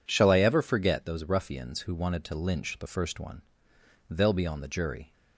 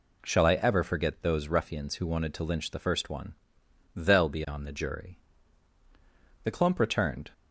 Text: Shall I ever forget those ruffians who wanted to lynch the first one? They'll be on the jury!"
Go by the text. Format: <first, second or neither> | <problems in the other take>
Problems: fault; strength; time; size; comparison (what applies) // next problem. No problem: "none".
first | goes on to say "The clump returned"; noticeable; from 6.4 s on; 0.88 s long